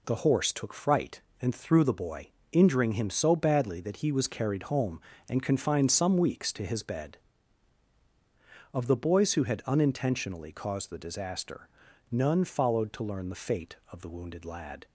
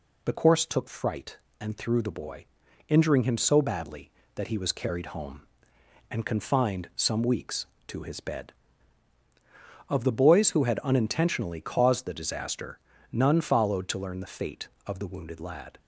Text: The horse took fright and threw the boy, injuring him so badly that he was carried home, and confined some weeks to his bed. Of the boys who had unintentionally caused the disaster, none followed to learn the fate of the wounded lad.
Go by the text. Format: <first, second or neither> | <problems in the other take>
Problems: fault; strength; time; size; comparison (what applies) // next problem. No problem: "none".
first | says "course" for "horse"; at 0.3 s